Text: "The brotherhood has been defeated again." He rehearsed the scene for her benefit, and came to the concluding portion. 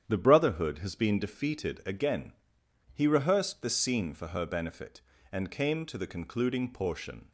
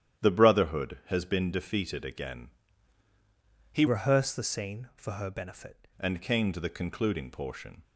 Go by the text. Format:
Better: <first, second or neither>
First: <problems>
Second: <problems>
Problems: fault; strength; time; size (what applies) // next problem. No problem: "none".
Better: first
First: starts louder than the rest; strong; until 1.0 s; 9.5 dB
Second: starts louder than the rest; strong; until 1.2 s; 10.5 dB // changes voice from "rehearsed" to "benefit"; from 3.8 to 5.8 s; 2.0 s long